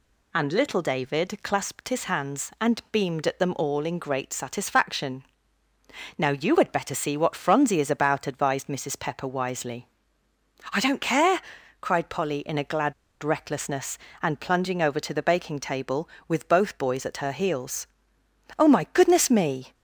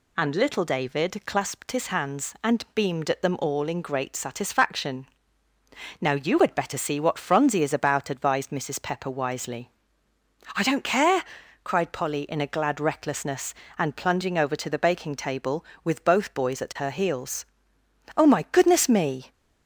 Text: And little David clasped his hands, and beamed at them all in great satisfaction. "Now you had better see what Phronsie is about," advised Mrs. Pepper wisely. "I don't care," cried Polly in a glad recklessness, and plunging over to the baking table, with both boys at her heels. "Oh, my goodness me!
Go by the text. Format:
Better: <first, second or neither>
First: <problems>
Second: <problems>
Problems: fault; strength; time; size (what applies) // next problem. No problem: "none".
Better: second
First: pauses between "glad" and "recklessness"; slight; at 12.9 s; 0.28 s long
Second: none